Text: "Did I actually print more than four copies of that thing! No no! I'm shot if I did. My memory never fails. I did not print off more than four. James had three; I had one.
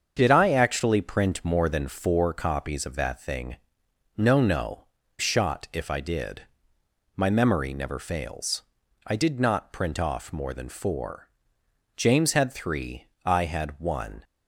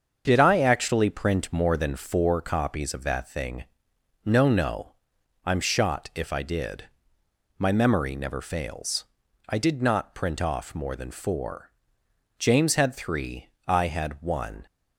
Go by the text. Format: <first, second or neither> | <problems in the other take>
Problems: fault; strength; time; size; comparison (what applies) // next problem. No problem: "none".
second | starts louder than the rest; until 1.1 s; 7 dB; also in the second // skips "I'm"; at 5.0 s